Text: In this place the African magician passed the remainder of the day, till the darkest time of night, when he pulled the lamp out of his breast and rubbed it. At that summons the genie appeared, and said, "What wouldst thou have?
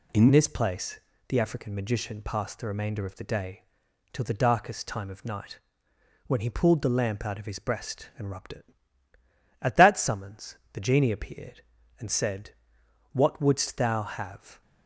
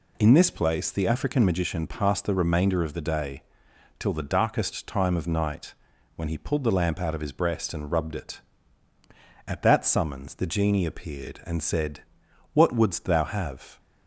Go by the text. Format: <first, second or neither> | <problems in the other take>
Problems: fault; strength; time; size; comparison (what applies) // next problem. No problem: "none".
second | changes voice at "this"; from 0.3 s on; 14.3 s long // pauses between "place" and "the"; slight; at 1.0 s; 0.28 s long